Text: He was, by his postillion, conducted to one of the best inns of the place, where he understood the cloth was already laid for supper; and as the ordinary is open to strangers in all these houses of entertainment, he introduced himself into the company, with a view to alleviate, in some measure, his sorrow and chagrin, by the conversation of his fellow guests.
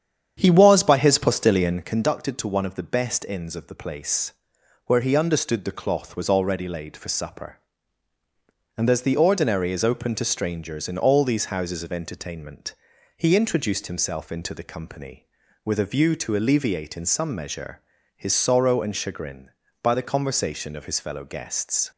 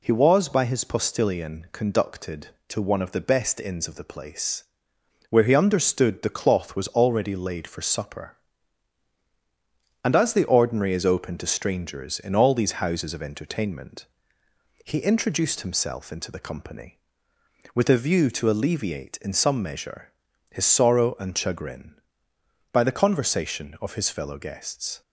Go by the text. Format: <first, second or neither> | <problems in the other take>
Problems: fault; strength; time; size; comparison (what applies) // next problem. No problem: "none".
second | starts louder than the rest; strong; until 2.0 s; 8.5 dB